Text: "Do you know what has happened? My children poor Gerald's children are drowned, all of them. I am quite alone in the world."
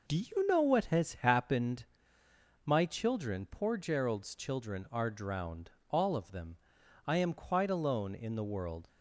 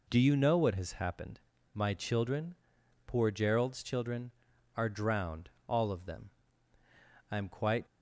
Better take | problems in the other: first | pauses between "children" and "poor"; noticeable; at 2.5 s; 0.52 s long // stops before "alone in the world"; at 7.8 s

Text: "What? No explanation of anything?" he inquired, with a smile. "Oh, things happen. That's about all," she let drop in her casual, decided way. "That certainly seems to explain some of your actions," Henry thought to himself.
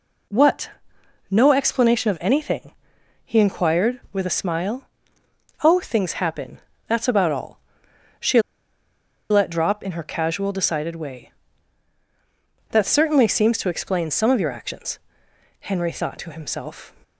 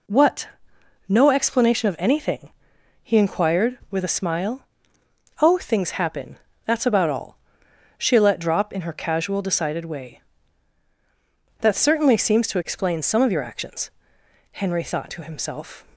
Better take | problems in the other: second | pauses between "she" and "let"; noticeable; at 8.4 s; 0.88 s long

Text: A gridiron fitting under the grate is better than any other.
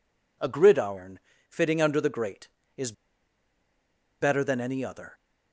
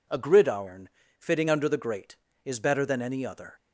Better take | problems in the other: second | pauses between "gridiron" and "fitting"; slight; at 1.1 s; 0.32 s long; slight in the second // pauses between "is" and "better"; strong; at 2.9 s; 1.2 s long

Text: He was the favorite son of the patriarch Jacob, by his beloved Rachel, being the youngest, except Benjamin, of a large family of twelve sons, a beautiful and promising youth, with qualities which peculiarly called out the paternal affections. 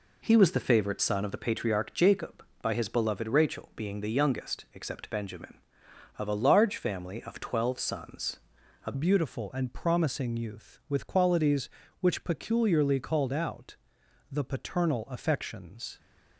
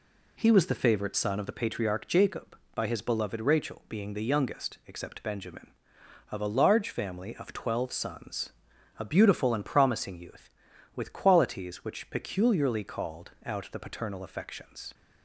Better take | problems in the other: second | changes voice at "beautiful"; from 8.9 s on; 7.0 s long // pauses between "out" and "the"; noticeable; at 13.7 s; 0.54 s long

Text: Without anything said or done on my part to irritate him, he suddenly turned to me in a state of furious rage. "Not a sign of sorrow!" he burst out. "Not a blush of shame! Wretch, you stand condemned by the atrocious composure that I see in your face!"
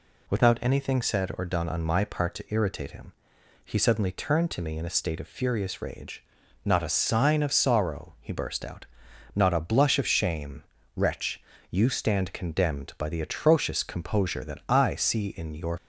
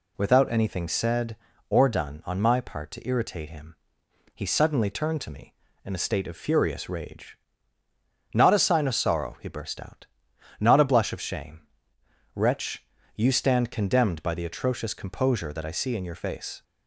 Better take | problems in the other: second | stops before "face"; at 15.7 s

